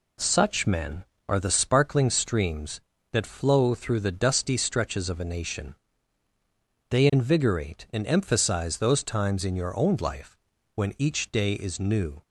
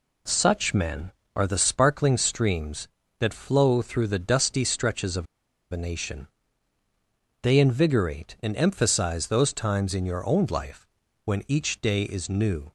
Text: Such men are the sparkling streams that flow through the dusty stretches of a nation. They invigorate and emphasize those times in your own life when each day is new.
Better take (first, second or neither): first